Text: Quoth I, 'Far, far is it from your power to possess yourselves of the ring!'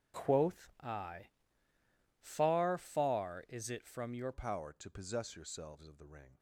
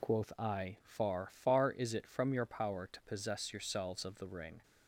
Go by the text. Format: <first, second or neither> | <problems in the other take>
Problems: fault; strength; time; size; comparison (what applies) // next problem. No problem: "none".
second | starts louder than the rest; strong; until 1.2 s; 8.5 dB // changes voice at "power"; from 4.3 s on; 2.0 s long